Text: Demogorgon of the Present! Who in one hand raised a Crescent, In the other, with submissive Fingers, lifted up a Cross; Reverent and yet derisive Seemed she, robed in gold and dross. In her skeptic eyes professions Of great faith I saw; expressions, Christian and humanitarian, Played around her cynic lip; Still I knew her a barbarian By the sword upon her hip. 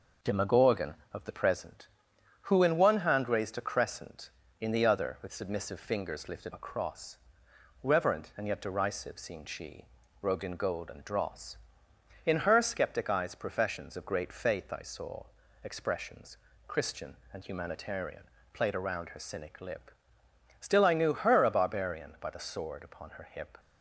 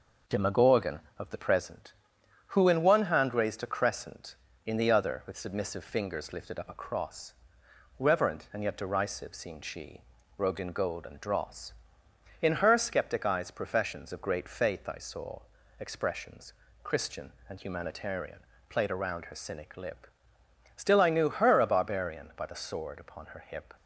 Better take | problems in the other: second | skips "up"; at 6.5 s

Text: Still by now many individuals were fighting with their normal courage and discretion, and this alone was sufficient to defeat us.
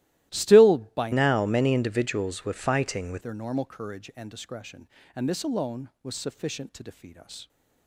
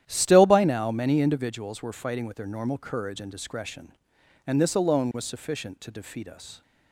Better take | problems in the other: second | starts louder than the rest; strong; until 1.3 s; 15.5 dB; strong in the second // changes voice from "now" to "with"; from 1.1 to 3.2 s; 2.1 s long

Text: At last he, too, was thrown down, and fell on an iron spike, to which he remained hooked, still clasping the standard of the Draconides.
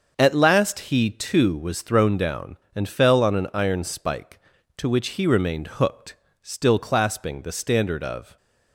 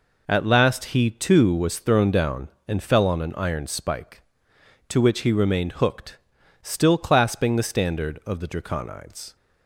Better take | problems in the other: second | starts louder than the rest; until 1.1 s; 6.5 dB // stops before "the Draconides"; at 8.3 s

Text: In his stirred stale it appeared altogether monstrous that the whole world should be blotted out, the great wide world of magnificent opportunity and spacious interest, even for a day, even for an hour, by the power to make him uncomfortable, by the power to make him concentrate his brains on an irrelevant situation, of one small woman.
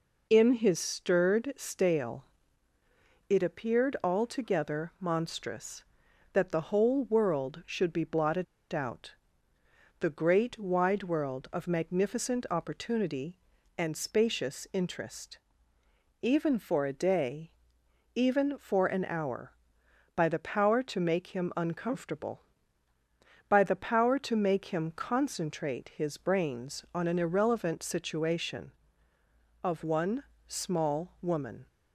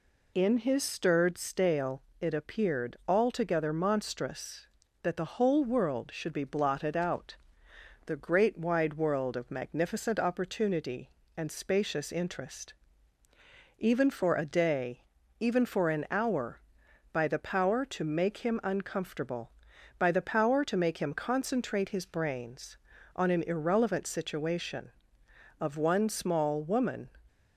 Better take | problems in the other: second | pauses between "stale" and "it"; at 2.2 s; 1.0 s long; slight in the second // pauses between "blotted" and "out"; slight; at 8.4 s; 0.27 s long // pauses between "one" and "small"; slight; at 30.2 s; 0.24 s long

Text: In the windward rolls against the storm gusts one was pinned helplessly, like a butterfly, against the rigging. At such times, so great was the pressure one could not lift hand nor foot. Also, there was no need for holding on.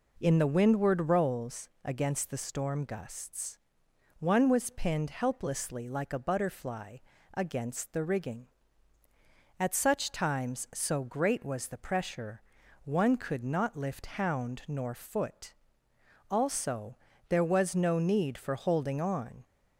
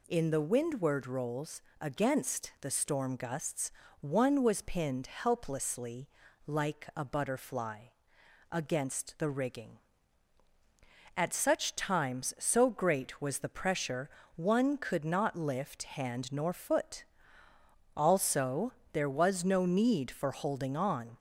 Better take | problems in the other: second | pauses between "rolls" and "against"; slight; at 1.6 s; 0.16 s long; slight in the second // pauses between "gusts" and "one"; noticeable; at 3.5 s; 0.60 s long; slight in the second // pauses between "pressure" and "one"; at 12.4 s; 0.42 s long; slight in the second // says "hound" for "hand"; at 14.0 s

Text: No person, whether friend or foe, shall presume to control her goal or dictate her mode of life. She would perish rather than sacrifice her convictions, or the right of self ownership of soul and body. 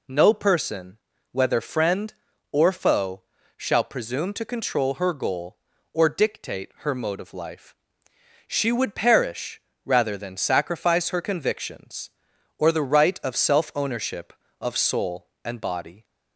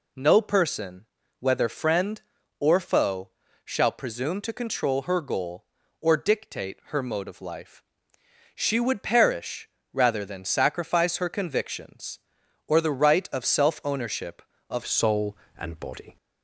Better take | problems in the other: first | pauses between "perish" and "rather"; slight; at 9.6 s; 0.24 s long; slight in the first // changes voice at "soul"; from 14.8 s on; 1.3 s long

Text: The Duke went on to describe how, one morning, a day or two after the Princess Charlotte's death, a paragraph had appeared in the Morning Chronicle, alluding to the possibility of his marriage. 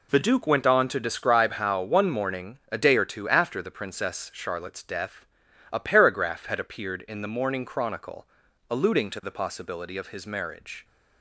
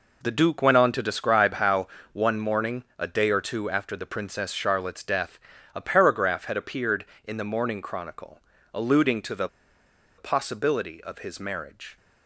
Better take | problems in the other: first | pauses between "the" and "possibility"; noticeable; at 9.4 s; 0.70 s long

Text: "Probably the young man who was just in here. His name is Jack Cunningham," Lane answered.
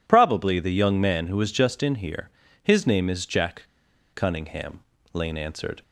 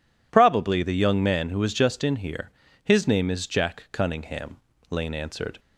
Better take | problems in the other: second | pauses between "Jack" and "Cunningham"; noticeable; at 3.6 s; 0.46 s long

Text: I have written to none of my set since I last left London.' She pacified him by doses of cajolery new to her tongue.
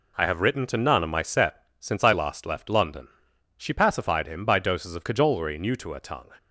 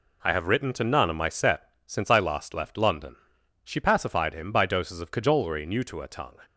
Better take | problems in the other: neither | pauses between "set" and "since"; slight; the same in both

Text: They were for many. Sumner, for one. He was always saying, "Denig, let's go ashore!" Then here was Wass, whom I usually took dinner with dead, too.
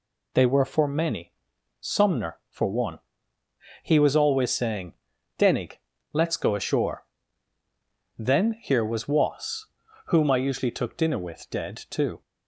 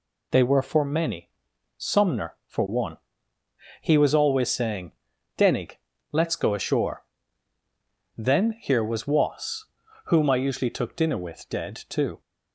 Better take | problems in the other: neither | none

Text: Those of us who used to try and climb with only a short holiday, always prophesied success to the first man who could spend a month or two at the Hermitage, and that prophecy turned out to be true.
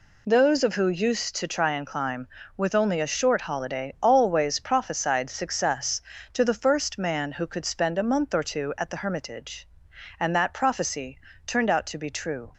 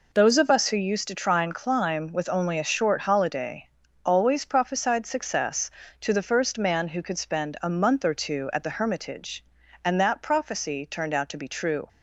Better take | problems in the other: second | skips "us"; at 0.7 s // pauses between "prophecy" and "turned"; slight; at 11.1 s; 0.30 s long

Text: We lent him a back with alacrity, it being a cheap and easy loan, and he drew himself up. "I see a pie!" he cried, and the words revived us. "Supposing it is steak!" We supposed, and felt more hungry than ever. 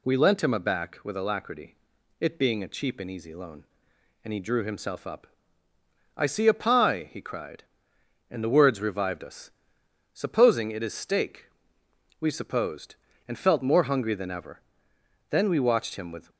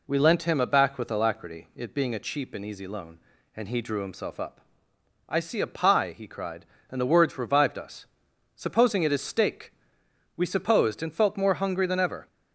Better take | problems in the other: second | goes on to say "Then we watched him with"; noticeable; from 15.2 s on; 1.0 s long

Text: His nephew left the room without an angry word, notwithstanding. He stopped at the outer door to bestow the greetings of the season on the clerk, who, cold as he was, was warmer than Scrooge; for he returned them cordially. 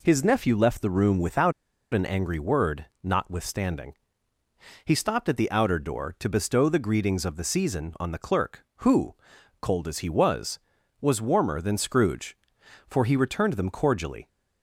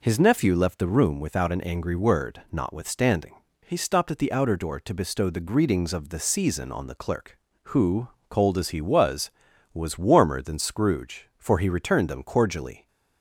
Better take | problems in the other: second | pauses between "without" and "an"; at 1.5 s; 0.39 s long

